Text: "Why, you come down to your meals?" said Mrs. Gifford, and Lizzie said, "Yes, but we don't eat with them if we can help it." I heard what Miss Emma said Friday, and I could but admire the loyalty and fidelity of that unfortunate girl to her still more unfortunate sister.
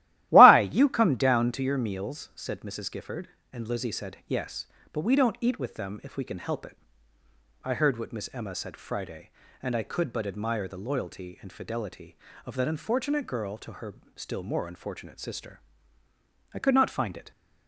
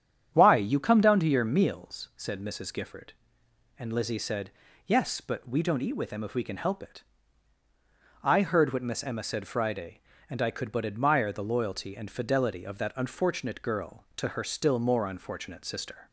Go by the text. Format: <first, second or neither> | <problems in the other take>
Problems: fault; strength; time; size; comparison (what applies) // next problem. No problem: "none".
second | starts louder than the rest; strong; until 1.3 s; 15 dB; strong in the second // pauses between "her" and "still"; slight; at 13.9 s; 0.22 s long // goes on to say "I could not find it"; noticeable; from 16.5 s on; 0.76 s long